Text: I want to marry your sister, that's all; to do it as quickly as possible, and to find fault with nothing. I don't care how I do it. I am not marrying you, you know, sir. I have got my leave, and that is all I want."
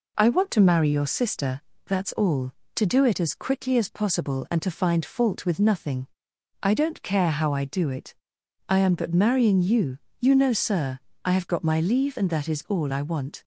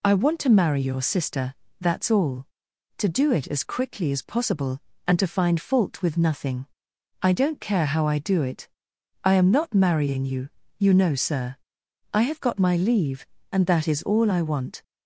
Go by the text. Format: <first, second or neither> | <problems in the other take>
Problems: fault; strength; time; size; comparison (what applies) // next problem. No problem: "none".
second | says "but" for "not"; at 8.9 s